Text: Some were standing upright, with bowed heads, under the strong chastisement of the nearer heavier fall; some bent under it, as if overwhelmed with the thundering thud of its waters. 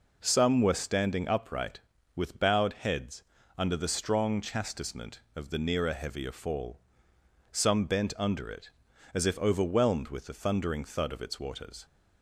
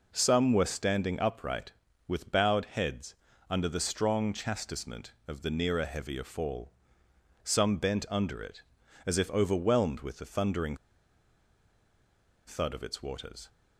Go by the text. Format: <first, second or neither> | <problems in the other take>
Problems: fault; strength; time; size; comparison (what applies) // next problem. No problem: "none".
first | pauses between "thundering" and "thud"; strong; at 10.7 s; 1.7 s long